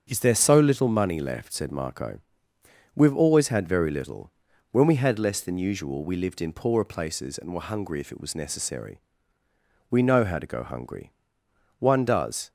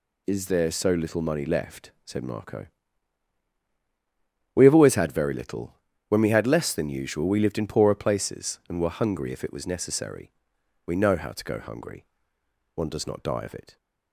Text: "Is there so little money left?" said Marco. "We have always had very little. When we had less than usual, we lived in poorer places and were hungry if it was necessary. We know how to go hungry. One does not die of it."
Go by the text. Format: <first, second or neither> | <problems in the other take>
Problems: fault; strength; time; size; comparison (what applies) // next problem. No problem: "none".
second | starts louder than the rest; strong; until 1.0 s; 7.5 dB // stops before "not die of it"; at 12.4 s